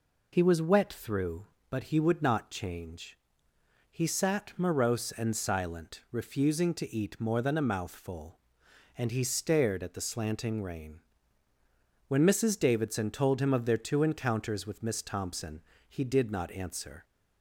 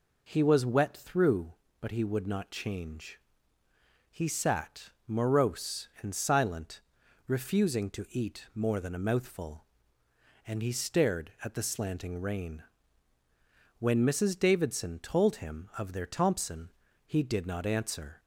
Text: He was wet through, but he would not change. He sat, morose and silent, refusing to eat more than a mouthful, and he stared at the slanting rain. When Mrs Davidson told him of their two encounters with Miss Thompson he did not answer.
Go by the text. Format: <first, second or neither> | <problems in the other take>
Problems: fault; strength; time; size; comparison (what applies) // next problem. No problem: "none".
first | skips "two encounters with Miss"; at 16.0 s // pauses between "Thompson" and "he"; slight; at 16.7 s; 0.34 s long; slight in the first